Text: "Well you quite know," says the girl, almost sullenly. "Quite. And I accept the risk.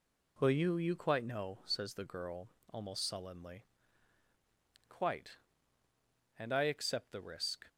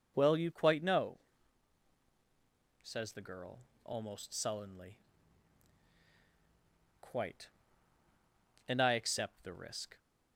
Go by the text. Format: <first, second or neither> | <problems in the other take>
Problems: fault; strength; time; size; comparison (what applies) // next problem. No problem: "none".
second | says "you" twice; at 0.7 s